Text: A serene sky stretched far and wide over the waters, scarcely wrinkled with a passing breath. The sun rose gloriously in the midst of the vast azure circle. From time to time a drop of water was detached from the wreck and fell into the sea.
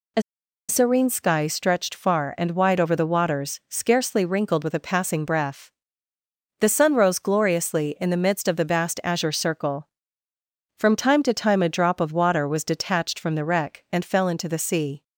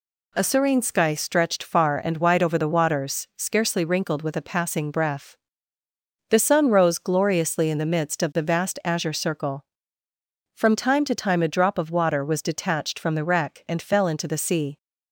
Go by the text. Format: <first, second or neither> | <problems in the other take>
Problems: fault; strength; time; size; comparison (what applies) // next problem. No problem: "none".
second | pauses between "A" and "serene"; noticeable; at 0.2 s; 0.46 s long